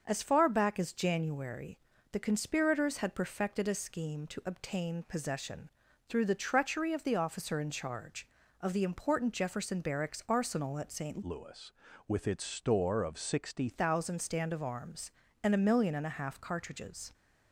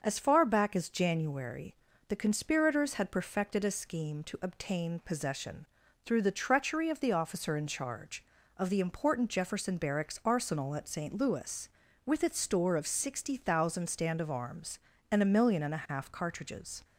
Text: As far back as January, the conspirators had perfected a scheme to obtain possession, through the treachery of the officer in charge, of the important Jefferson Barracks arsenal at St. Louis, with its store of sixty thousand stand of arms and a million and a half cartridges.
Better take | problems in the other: second | starts louder than the rest; until 1.0 s; 6 dB; also in the second // changes voice from "Louis" to "sixty"; from 11.2 to 13.6 s; 2.4 s long

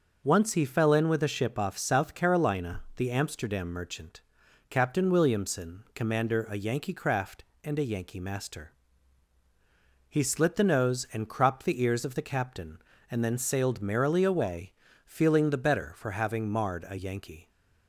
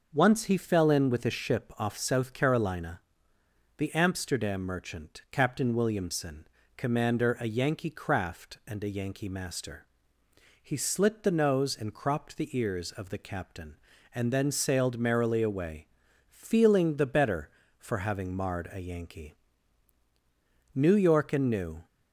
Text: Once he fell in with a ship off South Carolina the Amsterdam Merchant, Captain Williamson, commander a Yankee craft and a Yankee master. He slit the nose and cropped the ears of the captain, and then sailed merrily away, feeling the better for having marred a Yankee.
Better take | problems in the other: first | pauses between "Carolina" and "the"; noticeable; at 2.9 s; 0.78 s long // goes on to say "New York and New"; noticeable; from 20.7 s on; 1.1 s long

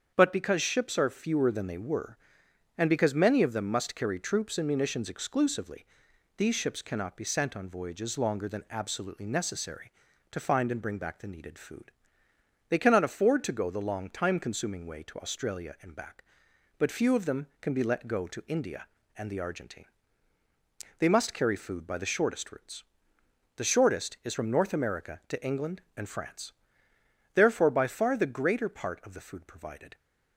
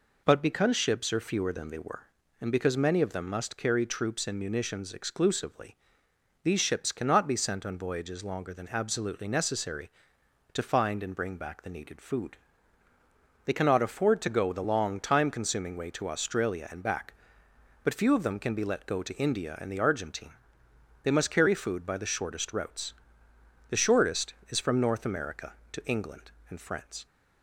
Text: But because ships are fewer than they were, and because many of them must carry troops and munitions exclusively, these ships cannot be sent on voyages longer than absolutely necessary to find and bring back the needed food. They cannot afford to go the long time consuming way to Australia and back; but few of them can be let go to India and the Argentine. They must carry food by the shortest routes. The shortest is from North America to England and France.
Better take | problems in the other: second | starts louder than the rest; strong; until 1.1 s; 7.5 dB // goes on to say "Therefore by far the greater part of the food provided"; strong; from 27.3 s on; 2.6 s long

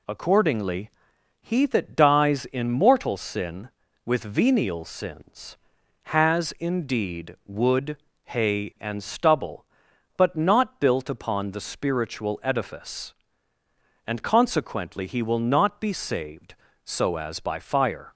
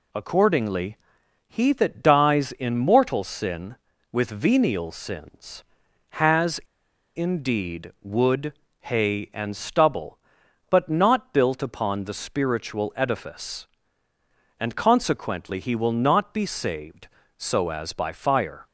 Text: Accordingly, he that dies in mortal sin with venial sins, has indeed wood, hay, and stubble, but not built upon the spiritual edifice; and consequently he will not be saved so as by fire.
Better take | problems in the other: first | pauses between "has" and "indeed"; noticeable; at 6.5 s; 0.57 s long

